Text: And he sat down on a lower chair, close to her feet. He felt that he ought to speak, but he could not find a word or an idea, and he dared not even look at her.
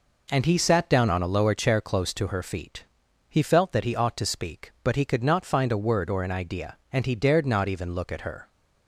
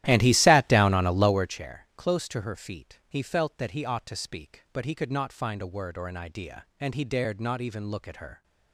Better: first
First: none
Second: starts louder than the rest; strong; until 1.6 s; 13.5 dB

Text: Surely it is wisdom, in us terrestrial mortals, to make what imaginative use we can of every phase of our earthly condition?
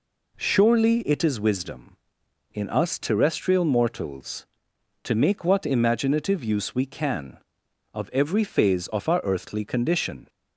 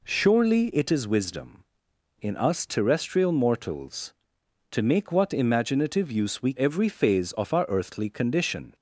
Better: first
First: none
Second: skips "can of"; at 6.5 s

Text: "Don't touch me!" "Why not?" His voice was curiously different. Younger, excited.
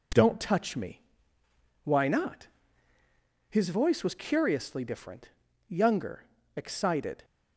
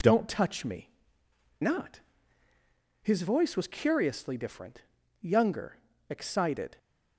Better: first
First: none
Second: skips "Why"; at 1.2 s

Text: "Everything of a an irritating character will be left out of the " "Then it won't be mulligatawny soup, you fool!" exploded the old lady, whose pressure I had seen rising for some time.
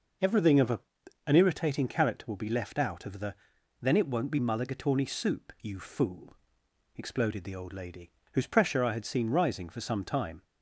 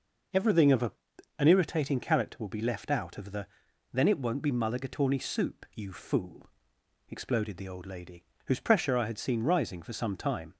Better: neither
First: pauses between "a" and "an"; noticeable; at 0.7 s; 0.48 s long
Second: pauses between "a" and "an"; noticeable; at 0.9 s; 0.48 s long

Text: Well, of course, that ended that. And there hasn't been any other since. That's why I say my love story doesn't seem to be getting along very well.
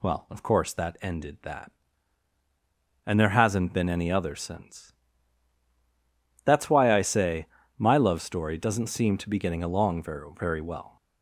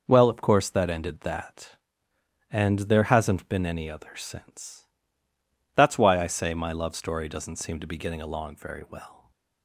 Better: second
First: pauses between "say" and "my"; slight; at 7.4 s; 0.32 s long // says "very" twice; at 10.3 s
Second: none

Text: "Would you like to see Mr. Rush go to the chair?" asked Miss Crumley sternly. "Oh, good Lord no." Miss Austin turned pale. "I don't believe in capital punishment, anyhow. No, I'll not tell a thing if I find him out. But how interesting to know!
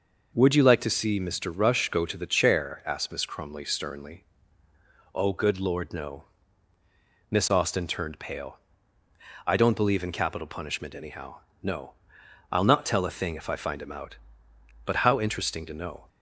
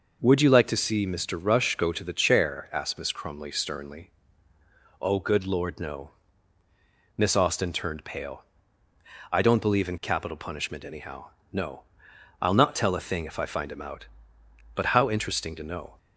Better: neither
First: none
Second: none

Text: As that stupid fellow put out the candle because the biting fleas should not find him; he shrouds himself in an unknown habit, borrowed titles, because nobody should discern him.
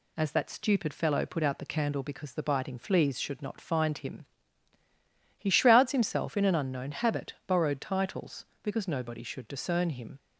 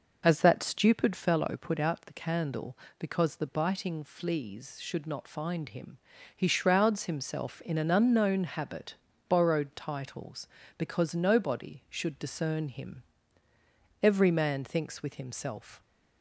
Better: first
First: none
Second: goes on to say "Every man thinks with himself"; strong; from 14.0 s on; 1.7 s long

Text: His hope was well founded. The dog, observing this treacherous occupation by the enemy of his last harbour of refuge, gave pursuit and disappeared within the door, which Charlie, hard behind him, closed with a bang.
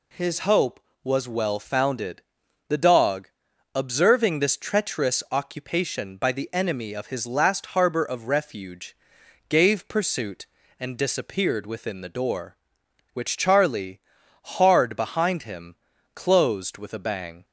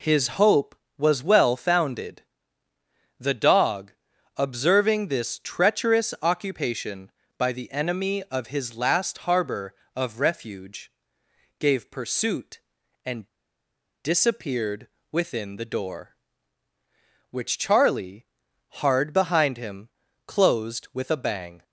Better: first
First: none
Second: pauses between "and" and "disappeared"; noticeable; at 13.2 s; 0.77 s long // pauses between "disappeared" and "within"; slight; at 14.8 s; 0.24 s long

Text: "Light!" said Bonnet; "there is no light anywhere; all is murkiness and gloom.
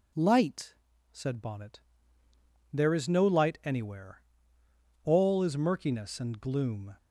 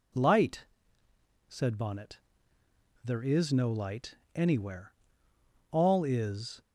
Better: first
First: none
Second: pauses between "light" and "anywhere"; slight; at 4.1 s; 0.18 s long // stops before "murkiness and gloom"; at 6.6 s

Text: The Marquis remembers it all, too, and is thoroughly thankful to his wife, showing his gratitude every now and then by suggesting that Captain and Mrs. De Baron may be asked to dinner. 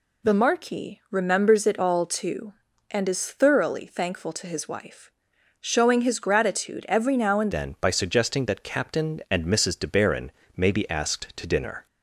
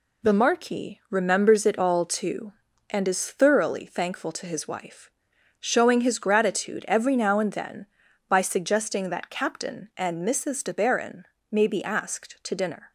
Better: second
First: changes voice at "then"; from 7.5 s on; 4.3 s long // pauses between "Baron" and "may"; slight; at 10.2 s; 0.28 s long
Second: pauses between "Baron" and "may"; slight; at 11.2 s; 0.26 s long

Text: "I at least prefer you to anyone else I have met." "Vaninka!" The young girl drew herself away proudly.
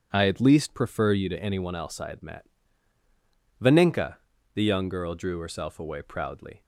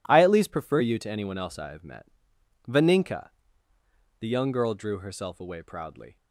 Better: second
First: says "had" for "have"; at 2.0 s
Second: none

